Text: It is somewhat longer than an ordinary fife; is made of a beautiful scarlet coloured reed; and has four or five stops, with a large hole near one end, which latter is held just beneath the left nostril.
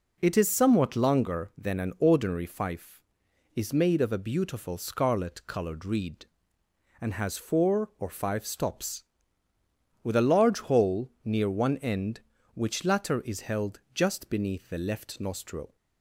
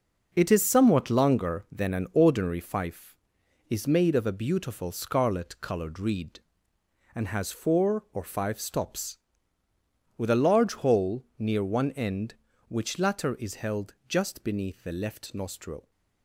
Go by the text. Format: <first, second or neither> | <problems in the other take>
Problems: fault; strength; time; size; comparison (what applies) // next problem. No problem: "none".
first | gets quieter; strong; throughout; 7.5 dB // pauses between "hole" and "near"; slight; at 11.2 s; 0.16 s long; slight in the first // pauses between "held" and "just"; slight; at 13.9 s; 0.16 s long; slight in the first